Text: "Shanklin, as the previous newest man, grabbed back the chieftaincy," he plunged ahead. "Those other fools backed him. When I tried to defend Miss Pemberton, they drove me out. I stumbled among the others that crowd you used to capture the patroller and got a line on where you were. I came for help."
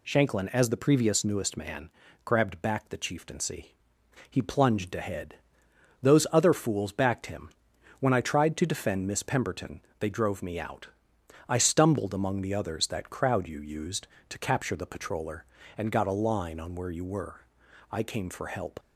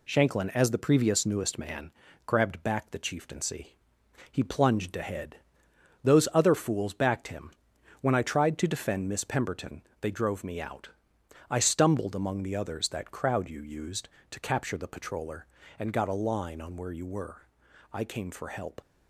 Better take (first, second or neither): first